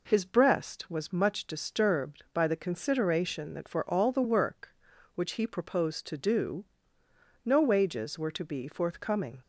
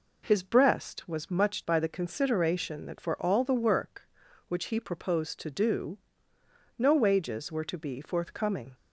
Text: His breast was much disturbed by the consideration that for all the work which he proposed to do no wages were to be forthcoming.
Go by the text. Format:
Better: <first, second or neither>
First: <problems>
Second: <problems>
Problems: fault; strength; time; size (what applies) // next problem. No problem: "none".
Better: first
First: pauses between "do" and "no"; noticeable; at 6.6 s; 0.80 s long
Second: skips "disturbed"; at 1.6 s // pauses between "do" and "no"; noticeable; at 5.9 s; 0.80 s long